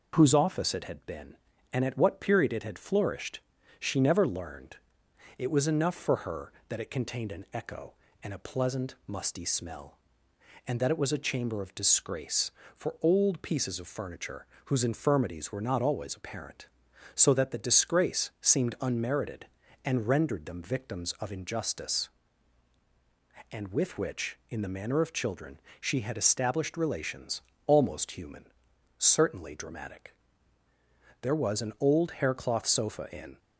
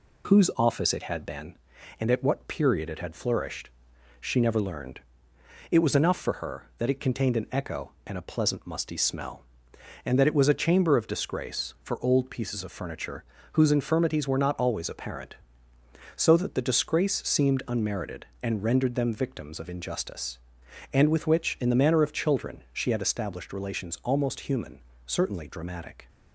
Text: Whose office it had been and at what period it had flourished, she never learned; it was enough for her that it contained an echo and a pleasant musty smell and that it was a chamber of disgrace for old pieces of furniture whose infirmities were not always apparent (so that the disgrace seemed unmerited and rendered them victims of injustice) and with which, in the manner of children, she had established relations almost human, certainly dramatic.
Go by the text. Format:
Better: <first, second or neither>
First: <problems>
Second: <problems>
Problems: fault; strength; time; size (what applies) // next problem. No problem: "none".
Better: second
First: pauses between "furniture" and "whose"; slight; at 14.4 s; 0.20 s long // pauses between "relations" and "almost"; slight; at 27.4 s; 0.24 s long // goes on to say "There was an old haircloth sofa in"; strong; from 31.2 s on; 2.1 s long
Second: pauses between "furniture" and "whose"; slight; at 13.2 s; 0.30 s long